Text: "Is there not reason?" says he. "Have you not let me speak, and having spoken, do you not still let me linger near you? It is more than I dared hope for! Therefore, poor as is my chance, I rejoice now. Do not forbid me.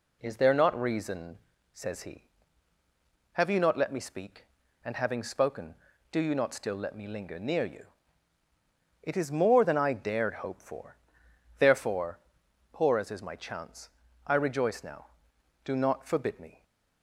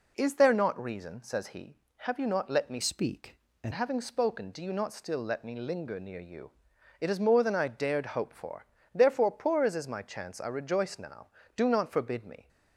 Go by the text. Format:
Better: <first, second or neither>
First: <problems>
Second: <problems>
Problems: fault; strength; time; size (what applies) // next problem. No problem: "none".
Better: first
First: none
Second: changes voice from "speak" to "and"; from 2.8 to 3.7 s; 0.9 s long